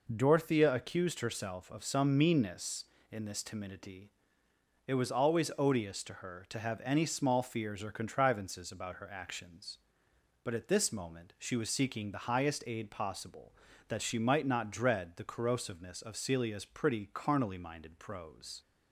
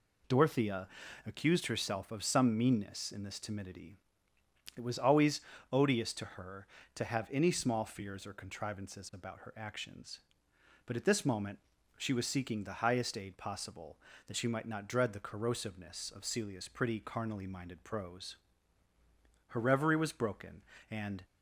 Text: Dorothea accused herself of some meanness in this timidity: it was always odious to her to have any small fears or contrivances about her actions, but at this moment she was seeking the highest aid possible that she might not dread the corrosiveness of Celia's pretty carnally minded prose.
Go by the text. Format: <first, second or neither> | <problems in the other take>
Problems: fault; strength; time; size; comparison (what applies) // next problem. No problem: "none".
first | pauses between "Dorothea" and "accused"; at 0.8 s; 0.38 s long // pauses between "always" and "odious"; slight; at 5.3 s; 0.32 s long // pauses between "moment" and "she"; at 11.5 s; 0.38 s long // goes on to say "Her reverie was broken and"; strong; from 19.4 s on; 1.7 s long